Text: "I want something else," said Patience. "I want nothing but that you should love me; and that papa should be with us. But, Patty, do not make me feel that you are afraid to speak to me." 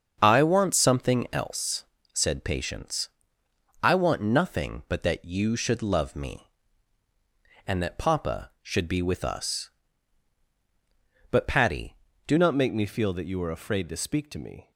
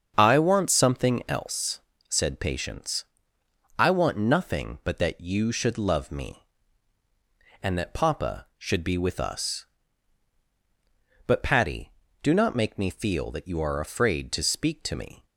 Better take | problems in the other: second | starts louder than the rest; until 1.2 s; 7 dB; also in the second // changes voice at "not"; from 12.3 s on; 2.4 s long

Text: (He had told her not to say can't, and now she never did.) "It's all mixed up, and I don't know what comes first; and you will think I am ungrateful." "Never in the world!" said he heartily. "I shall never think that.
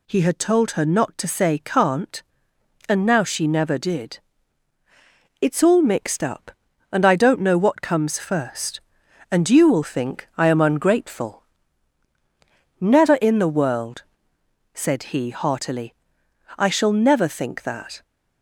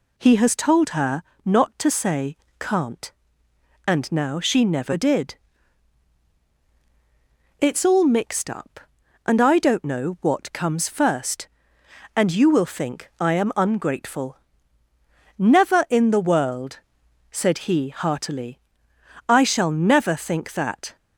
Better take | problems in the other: first | says "has" for "had"; at 0.3 s // pauses between "her" and "not"; slight; at 1.2 s; 0.24 s long // pauses between "say" and "can't"; slight; at 2.3 s; 0.24 s long

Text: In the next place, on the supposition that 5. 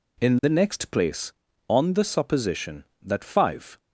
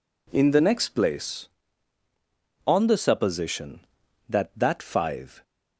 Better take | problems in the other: first | says "that" twice; at 4.5 s

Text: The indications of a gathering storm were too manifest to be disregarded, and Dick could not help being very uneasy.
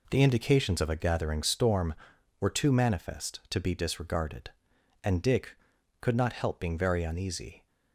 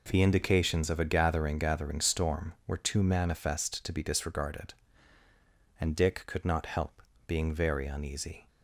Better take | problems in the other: first | says "gathering" twice; at 1.5 s // pauses between "help" and "being"; slight; at 7.0 s; 0.26 s long

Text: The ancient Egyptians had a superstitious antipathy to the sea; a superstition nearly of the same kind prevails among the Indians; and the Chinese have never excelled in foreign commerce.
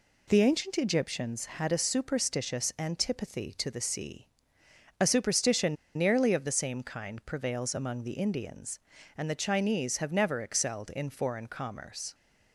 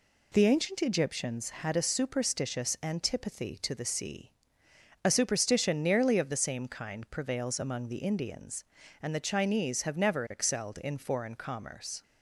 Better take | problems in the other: second | pauses between "superstition" and "nearly"; slight; at 5.7 s; 0.22 s long

